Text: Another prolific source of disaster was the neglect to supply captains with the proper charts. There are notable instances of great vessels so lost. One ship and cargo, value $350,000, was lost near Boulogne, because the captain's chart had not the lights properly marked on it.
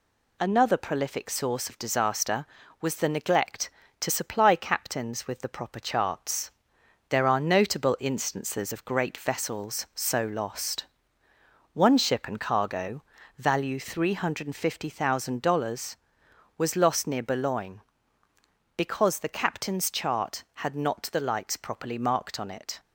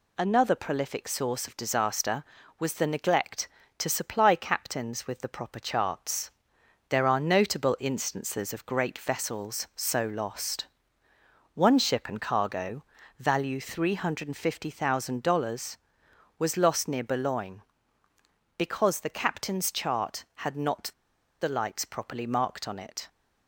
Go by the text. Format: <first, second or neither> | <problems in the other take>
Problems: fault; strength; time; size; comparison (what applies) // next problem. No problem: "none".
first | pauses between "not" and "the"; noticeable; at 20.9 s; 0.50 s long